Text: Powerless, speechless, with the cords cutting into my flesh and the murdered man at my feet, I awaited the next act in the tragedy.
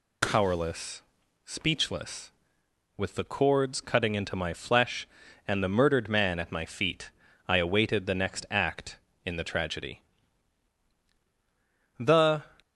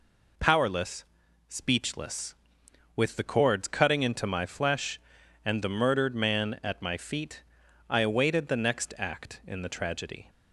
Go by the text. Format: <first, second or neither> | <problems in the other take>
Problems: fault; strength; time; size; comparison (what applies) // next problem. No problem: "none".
second | goes on to say "The"; from 11.9 s on; 0.54 s long